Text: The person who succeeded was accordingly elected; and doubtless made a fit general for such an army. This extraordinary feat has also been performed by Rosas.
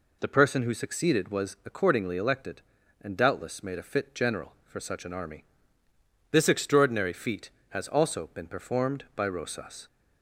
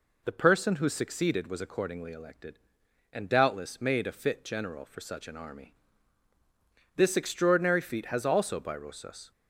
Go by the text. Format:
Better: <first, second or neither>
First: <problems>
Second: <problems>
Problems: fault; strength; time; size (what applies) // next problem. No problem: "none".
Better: first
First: none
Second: skips "been performed"; at 8.6 s